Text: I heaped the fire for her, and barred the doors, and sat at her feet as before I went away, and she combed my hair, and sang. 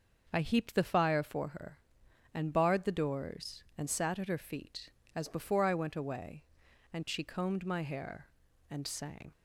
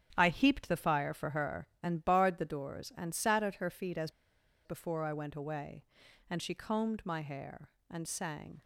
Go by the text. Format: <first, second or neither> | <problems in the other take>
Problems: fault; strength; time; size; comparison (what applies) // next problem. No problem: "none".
first | starts louder than the rest; strong; until 1.1 s; 9.5 dB; noticeable in the first // pauses between "as" and "before"; noticeable; at 4.1 s; 0.53 s long